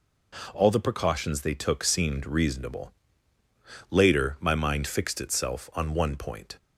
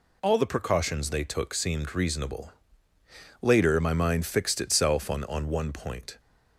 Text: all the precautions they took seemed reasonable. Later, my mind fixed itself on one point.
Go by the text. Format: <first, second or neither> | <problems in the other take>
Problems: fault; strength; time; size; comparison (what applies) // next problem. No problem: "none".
first | says "on" twice; at 5.2 s